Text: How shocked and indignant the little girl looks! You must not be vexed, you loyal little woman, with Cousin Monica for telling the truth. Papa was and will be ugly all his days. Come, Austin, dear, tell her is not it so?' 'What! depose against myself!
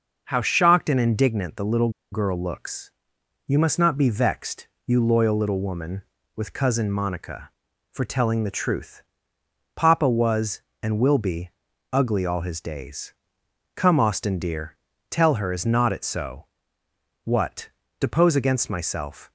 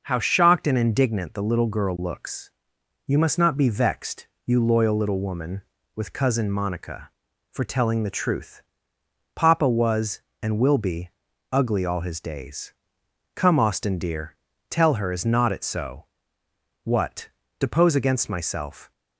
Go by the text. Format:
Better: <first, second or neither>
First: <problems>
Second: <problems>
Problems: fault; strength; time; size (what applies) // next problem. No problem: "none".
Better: second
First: starts louder than the rest; noticeable; until 1.2 s; 6 dB // pauses between "little" and "girl"; slight; at 1.9 s; 0.21 s long // pauses between "be" and "ugly"; at 11.4 s; 0.44 s long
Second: starts louder than the rest; noticeable; until 1.0 s; 6 dB // pauses between "be" and "ugly"; at 11.0 s; 0.44 s long